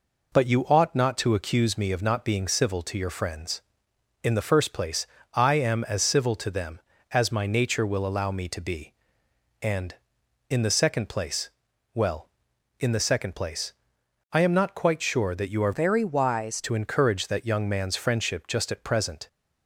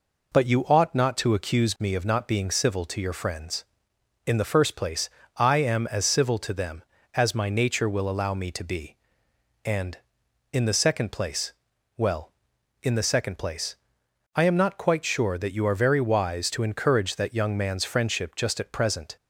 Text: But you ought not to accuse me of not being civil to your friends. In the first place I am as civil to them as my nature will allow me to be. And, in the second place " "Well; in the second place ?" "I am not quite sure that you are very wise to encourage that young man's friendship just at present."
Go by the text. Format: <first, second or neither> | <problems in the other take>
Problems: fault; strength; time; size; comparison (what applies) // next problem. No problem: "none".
second | pauses between "place" and "I"; slight; at 5.0 s; 0.30 s long; slight in the second // changes voice from "very" to "wise"; from 15.7 to 16.5 s; 0.8 s long